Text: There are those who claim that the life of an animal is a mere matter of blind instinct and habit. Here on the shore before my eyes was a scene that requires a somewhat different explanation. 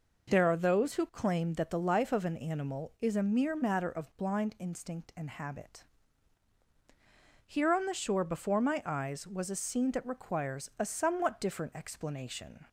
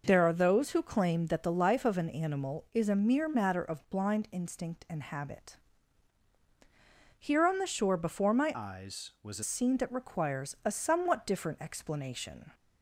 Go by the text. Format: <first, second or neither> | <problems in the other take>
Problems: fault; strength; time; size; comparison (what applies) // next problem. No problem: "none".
first | changes voice from "eyes" to "a"; from 8.5 to 9.4 s; 0.9 s long